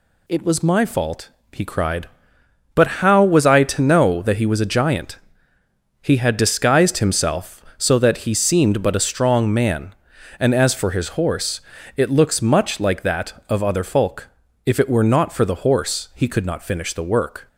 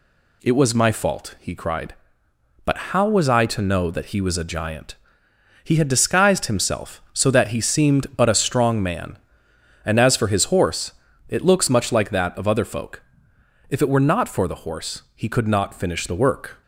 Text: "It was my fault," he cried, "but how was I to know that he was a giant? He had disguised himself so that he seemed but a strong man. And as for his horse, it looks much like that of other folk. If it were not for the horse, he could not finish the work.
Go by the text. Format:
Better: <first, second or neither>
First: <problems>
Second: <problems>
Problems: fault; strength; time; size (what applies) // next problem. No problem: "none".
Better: neither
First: none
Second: none